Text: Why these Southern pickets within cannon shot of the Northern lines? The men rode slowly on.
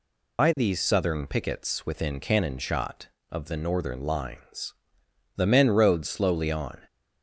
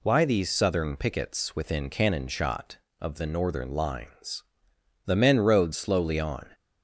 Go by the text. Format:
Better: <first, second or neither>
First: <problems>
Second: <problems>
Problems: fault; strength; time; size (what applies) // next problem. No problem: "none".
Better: second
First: loses the start of "Why"; at 0.3 s; 105 ms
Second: none